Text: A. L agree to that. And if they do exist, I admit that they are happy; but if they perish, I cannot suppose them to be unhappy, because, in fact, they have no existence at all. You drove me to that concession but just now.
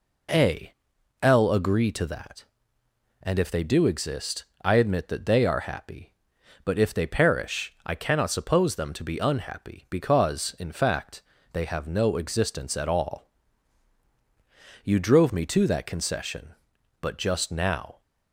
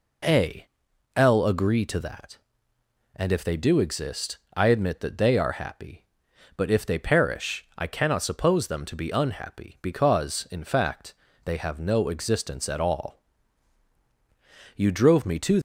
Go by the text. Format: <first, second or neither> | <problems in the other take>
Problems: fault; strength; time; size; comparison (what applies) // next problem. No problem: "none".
first | stops before "that concession but just now"; at 15.5 s